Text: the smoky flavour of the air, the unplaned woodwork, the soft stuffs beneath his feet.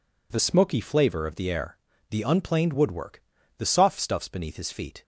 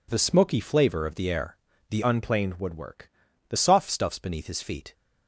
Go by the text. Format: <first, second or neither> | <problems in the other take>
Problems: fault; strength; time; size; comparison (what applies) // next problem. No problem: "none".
first | changes voice from "unplaned" to "the"; from 2.0 to 3.5 s; 1.5 s long